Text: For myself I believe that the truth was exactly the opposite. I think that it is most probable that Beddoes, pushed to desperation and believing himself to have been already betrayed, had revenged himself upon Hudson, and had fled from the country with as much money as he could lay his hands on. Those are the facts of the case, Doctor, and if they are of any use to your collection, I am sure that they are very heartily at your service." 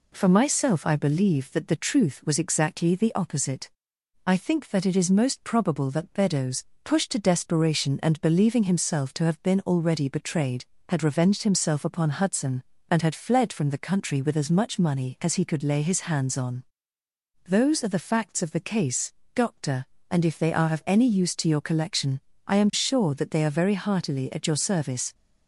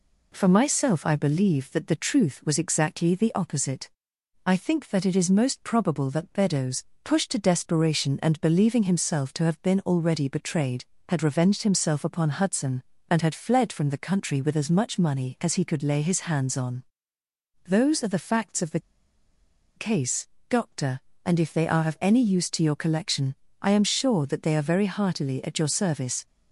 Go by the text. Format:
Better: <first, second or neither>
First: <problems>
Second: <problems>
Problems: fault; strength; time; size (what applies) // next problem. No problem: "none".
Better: first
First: none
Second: pauses between "the" and "case"; noticeable; at 18.8 s; 0.95 s long